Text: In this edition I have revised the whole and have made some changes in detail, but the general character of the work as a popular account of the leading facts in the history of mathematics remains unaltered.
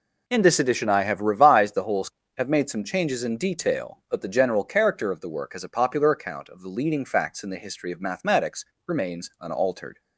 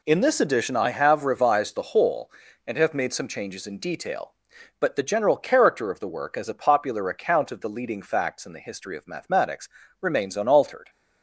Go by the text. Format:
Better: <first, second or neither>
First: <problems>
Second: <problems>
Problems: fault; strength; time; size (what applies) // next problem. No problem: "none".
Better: second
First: skips "and"; at 2.2 s // pauses between "mathematics" and "remains"; slight; at 8.6 s; 0.24 s long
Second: pauses between "mathematics" and "remains"; slight; at 9.6 s; 0.32 s long